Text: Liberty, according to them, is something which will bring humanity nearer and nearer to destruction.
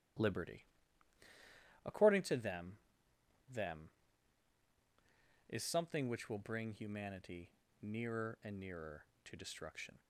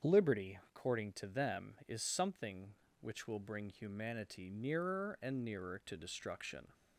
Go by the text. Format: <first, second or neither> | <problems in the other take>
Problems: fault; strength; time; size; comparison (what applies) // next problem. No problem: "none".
second | starts louder than the rest; strong; until 2.4 s; 12.5 dB; strong in the second // says "them" twice; at 3.4 s // pauses between "humanity" and "nearer"; slight; at 7.4 s; 0.32 s long